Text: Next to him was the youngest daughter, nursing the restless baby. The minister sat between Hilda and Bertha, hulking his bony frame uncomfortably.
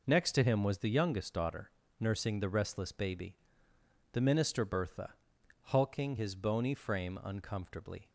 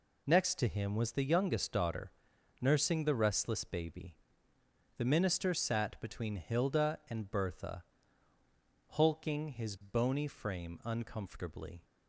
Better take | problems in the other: second | skips "sat between Hilda and"; at 4.6 s

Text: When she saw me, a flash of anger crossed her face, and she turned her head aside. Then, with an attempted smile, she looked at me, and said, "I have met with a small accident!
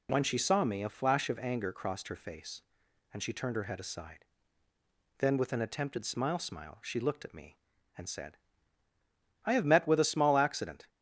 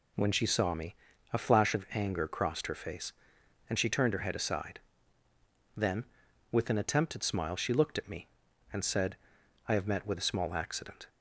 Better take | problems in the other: second | says "smile" twice; at 6.3 s

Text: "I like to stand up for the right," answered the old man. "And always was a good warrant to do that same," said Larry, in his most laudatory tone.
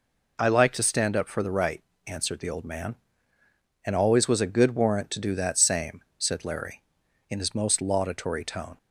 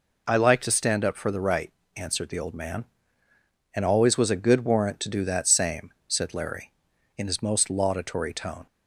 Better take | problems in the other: neither | none

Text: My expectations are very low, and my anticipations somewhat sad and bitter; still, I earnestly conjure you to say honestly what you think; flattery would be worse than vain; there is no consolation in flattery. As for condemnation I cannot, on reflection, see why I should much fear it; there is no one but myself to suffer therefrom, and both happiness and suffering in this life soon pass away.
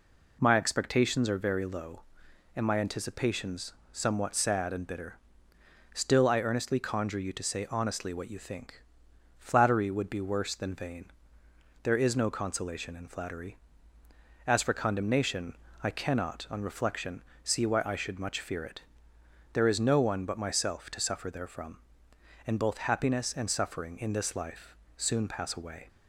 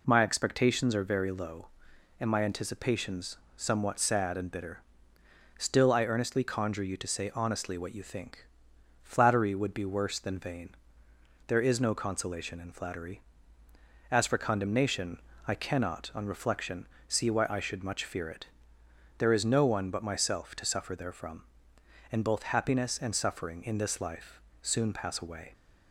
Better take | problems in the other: neither | pauses between "anticipations" and "somewhat"; slight; the same in both // pauses between "condemnation" and "I"; slight; the same in both // pauses between "life" and "soon"; slight; the same in both

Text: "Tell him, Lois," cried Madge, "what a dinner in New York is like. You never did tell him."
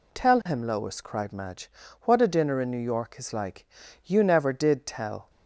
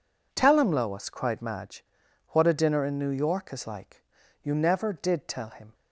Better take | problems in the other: second | stops before "him"; at 5.2 s

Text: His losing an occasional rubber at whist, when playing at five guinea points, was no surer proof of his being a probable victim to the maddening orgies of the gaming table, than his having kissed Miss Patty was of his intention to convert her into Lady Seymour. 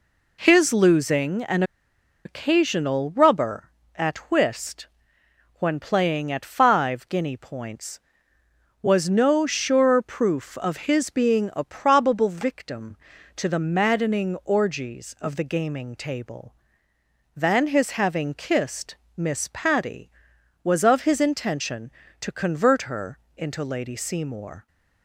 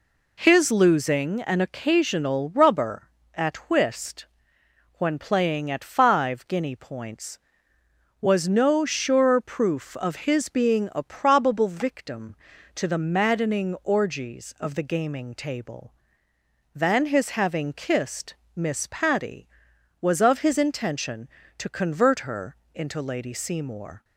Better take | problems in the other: second | pauses between "an" and "occasional"; noticeable; at 1.6 s; 0.63 s long // pauses between "kissed" and "Miss"; slight; at 18.9 s; 0.18 s long; slight in the second // pauses between "her" and "into"; slight; at 23.1 s; 0.18 s long; slight in the second

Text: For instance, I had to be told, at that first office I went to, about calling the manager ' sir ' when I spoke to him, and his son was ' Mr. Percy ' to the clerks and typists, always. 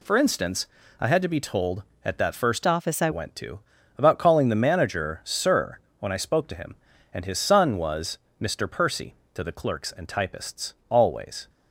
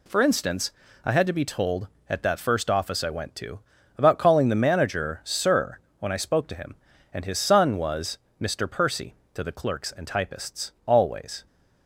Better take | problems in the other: second | changes voice from "office" to "I"; from 2.6 to 3.0 s; 0.4 s long

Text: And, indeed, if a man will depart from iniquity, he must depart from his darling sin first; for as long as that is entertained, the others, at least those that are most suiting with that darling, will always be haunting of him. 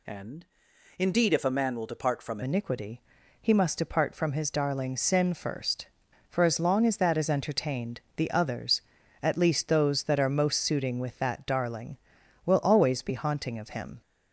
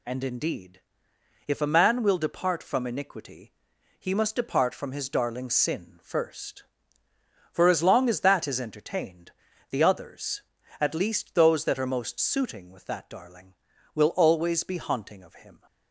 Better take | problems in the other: second | changes voice at "iniquity"; from 2.4 s on; 11.6 s long

